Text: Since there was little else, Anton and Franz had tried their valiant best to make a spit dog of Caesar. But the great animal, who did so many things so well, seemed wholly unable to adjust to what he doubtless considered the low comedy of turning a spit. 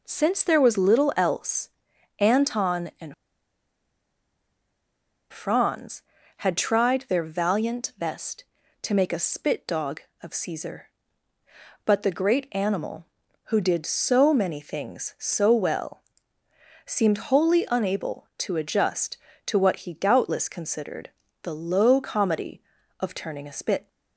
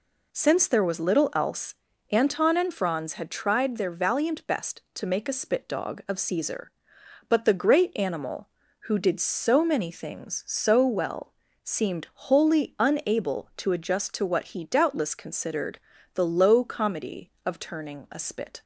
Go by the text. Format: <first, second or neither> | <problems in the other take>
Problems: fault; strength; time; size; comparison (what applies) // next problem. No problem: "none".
second | pauses between "and" and "Franz"; strong; at 3.1 s; 2.1 s long // pauses between "considered" and "the"; slight; at 21.0 s; 0.34 s long; slight in the second